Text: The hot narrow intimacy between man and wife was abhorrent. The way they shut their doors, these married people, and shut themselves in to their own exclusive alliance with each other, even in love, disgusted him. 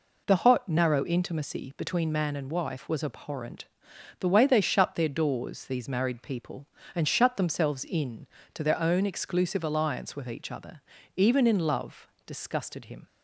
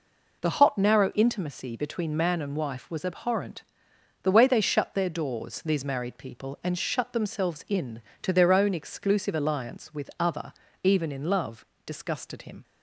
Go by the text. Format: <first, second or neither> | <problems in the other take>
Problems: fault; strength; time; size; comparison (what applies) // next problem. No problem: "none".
first | skips "each"; at 10.1 s